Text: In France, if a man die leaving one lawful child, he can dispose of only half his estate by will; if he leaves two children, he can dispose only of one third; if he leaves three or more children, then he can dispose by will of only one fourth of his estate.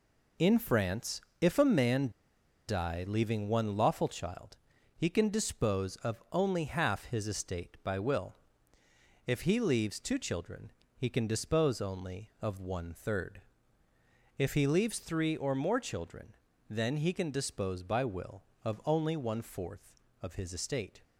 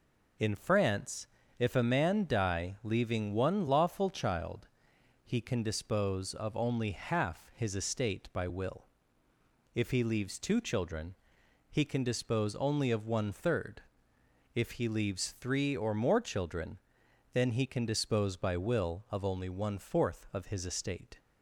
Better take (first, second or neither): second